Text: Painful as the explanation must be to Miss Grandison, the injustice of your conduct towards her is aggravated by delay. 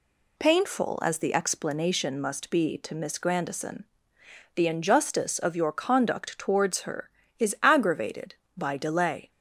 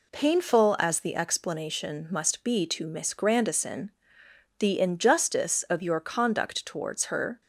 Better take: first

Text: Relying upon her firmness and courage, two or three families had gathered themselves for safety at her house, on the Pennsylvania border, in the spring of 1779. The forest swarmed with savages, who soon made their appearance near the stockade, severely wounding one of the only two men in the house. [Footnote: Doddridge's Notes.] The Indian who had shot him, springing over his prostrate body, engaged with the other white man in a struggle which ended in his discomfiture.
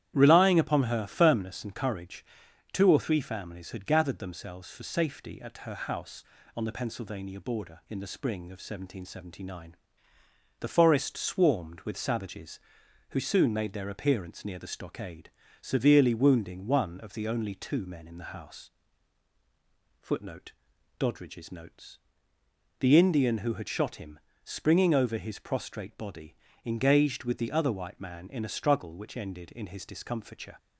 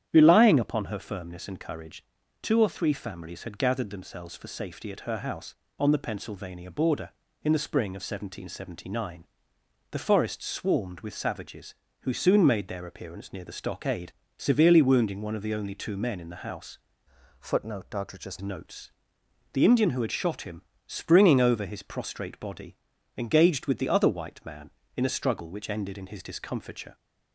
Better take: first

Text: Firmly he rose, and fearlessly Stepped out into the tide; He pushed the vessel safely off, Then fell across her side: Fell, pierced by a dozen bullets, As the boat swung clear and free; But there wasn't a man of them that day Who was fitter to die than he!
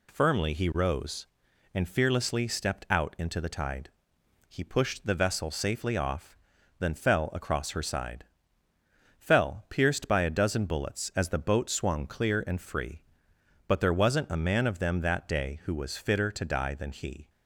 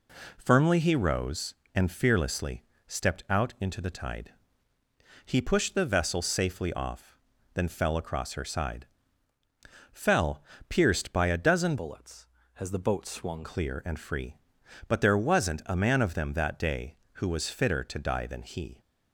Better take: first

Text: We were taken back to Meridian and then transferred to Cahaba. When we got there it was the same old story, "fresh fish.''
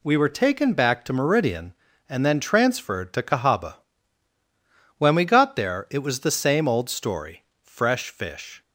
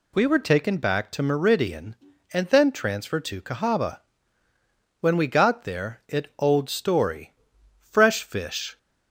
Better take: first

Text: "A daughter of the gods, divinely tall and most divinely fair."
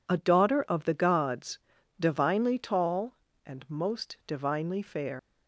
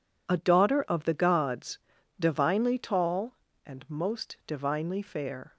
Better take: second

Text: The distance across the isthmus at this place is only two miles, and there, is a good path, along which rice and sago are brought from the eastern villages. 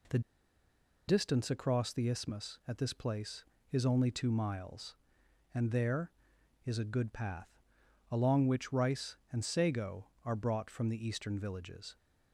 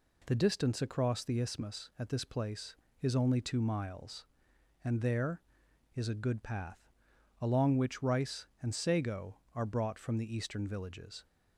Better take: second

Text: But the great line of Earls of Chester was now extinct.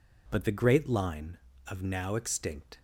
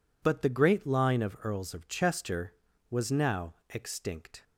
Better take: second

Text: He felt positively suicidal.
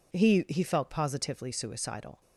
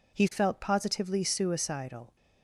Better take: second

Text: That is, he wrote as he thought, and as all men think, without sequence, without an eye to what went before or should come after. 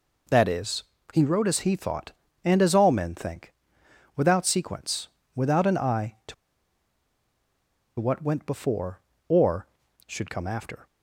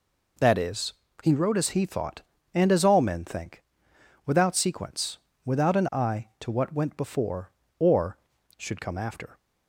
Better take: second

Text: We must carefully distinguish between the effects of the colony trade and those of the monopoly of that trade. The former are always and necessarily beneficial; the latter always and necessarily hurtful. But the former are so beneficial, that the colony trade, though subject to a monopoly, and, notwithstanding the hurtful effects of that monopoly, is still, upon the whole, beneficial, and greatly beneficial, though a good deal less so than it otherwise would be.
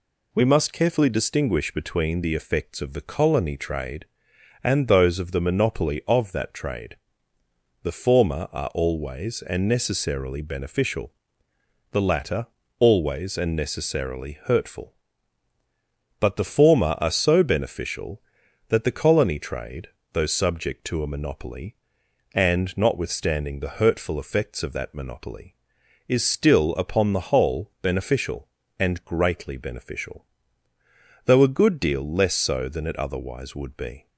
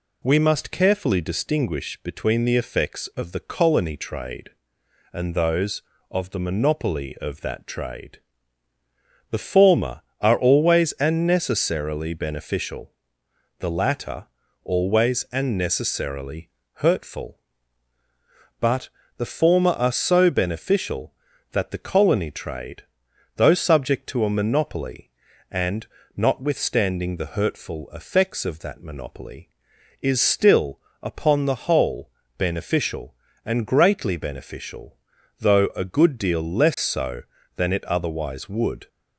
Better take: first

